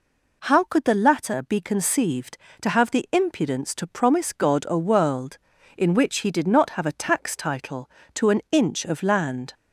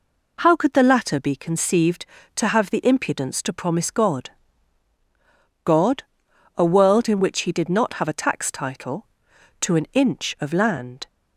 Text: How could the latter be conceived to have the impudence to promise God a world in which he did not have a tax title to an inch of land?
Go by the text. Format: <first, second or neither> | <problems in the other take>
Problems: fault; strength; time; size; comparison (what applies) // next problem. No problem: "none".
first | says "God" twice; at 5.6 s